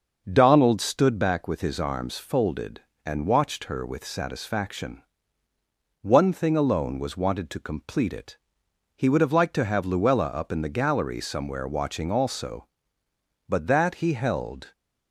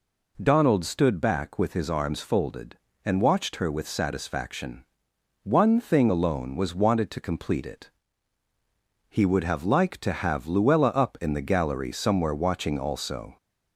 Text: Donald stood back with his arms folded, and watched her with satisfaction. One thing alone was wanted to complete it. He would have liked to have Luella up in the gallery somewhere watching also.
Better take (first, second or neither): second